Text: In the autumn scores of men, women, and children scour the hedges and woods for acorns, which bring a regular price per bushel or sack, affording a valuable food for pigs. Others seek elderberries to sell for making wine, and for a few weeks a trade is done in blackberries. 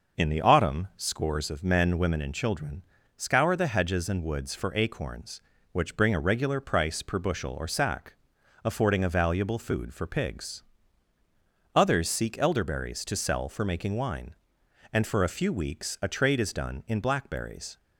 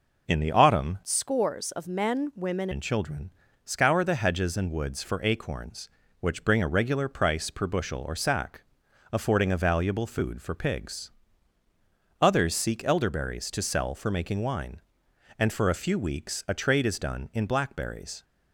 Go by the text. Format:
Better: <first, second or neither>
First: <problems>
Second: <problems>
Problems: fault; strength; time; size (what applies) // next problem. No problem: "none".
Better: first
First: pauses between "children" and "scour"; slight; at 2.8 s; 0.34 s long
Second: changes voice from "scores" to "women"; from 1.0 to 2.6 s; 1.6 s long // pauses between "children" and "scour"; slight; at 3.3 s; 0.34 s long